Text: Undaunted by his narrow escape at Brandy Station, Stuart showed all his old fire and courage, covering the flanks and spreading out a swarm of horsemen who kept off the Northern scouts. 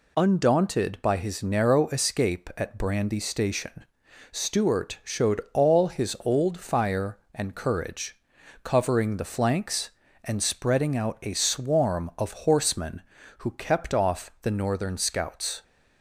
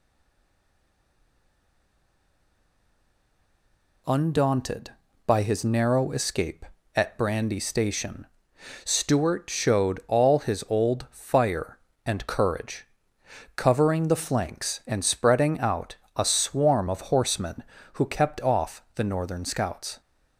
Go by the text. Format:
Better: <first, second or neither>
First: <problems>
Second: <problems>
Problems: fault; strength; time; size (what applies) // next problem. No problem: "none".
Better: first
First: none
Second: stays silent before the first word; strong; until 4.0 s; 4.0 s long // pauses between "out" and "a"; slight; at 15.9 s; 0.22 s long